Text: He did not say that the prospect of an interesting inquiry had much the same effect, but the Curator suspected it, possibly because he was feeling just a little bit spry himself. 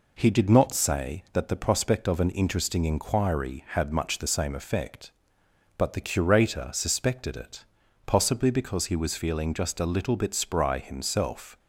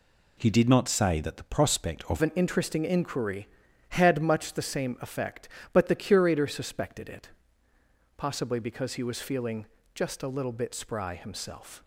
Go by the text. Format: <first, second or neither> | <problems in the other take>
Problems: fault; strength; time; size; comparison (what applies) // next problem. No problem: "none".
first | changes voice at "an"; from 2.2 s on; 9.6 s long // pauses between "feeling" and "just"; slight; at 9.6 s; 0.28 s long